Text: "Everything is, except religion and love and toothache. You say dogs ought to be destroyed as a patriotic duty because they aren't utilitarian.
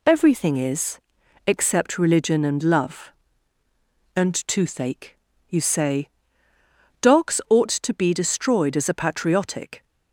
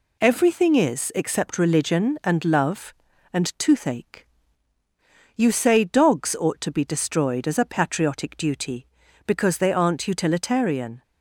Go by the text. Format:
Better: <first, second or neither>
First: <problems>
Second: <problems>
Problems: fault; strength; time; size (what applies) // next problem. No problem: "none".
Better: second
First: pauses between "say" and "dogs"; noticeable; at 6.0 s; 0.94 s long // stops before "duty because they aren't utilitarian"; at 9.8 s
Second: none